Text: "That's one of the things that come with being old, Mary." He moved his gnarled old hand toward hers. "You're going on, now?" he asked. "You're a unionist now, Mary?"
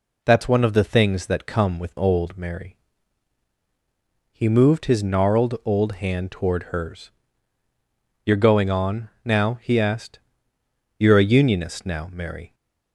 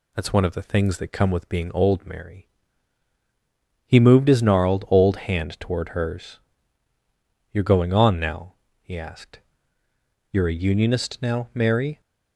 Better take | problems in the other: second | skips "being"; at 1.9 s

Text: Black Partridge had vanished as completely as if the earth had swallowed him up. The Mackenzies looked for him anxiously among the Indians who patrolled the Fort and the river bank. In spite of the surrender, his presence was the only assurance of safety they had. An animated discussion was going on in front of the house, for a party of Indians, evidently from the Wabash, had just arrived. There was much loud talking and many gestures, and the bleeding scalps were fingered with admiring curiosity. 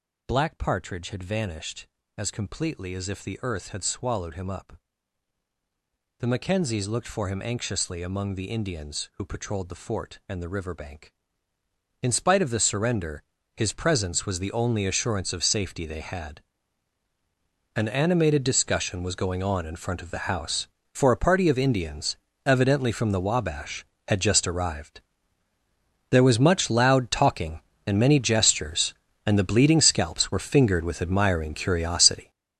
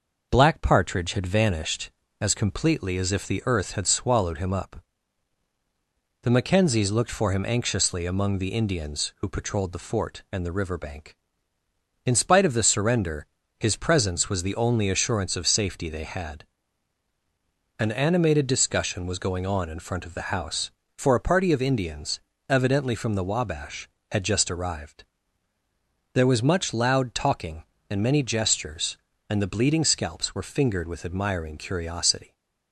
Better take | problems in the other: second | gets louder; strong; throughout; 10 dB

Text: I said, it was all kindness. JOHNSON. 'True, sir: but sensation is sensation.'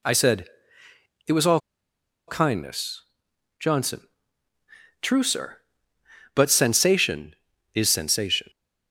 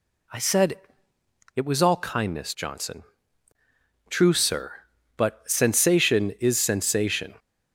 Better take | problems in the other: second | pauses between "all" and "kindness"; noticeable; at 1.5 s; 0.68 s long

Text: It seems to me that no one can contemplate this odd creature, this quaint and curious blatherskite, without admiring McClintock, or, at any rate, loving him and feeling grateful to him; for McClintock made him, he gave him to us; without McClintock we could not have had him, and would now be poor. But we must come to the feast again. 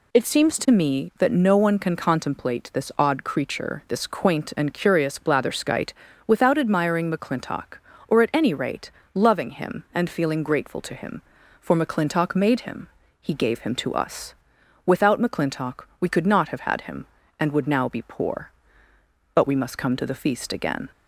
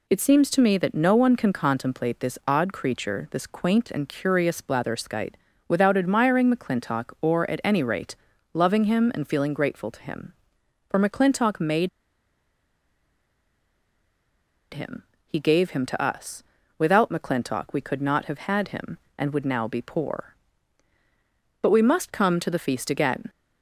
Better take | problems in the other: first | pauses between "made" and "him"; strong; at 11.8 s; 2.8 s long

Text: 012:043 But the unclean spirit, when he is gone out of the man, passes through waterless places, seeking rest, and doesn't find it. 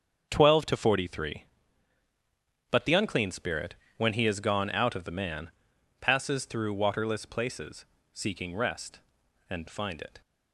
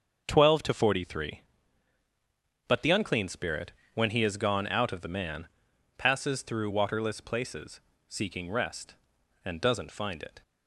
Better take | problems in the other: second | starts louder than the rest; until 1.3 s; 7 dB; also in the second // skips "doesn't"; at 9.6 s

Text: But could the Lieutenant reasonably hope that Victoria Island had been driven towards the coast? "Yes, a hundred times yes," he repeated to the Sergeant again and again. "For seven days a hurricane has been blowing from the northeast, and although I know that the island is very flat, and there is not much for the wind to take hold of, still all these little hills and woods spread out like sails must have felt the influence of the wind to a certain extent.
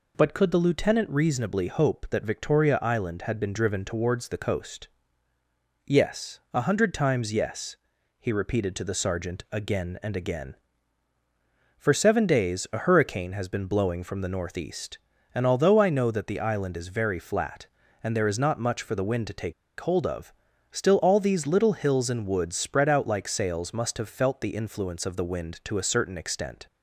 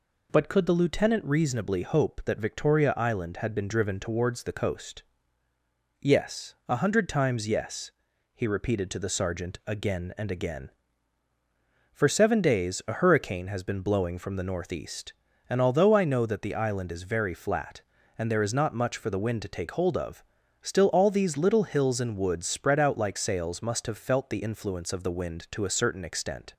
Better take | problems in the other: second | pauses between "take" and "hold"; slight; at 19.5 s; 0.26 s long

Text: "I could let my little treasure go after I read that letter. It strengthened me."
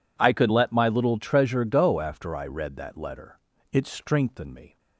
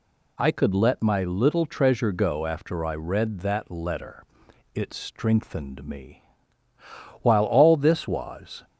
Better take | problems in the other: first | goes on to say "While all this was"; from 7.2 s on; 1.4 s long

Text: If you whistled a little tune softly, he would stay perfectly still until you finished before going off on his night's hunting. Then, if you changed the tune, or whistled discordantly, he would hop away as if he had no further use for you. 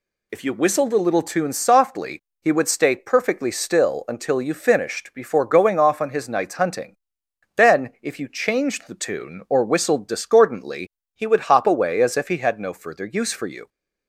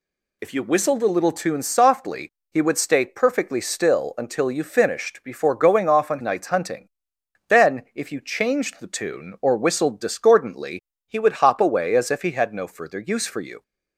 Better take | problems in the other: first | skips "his"; at 6.1 s

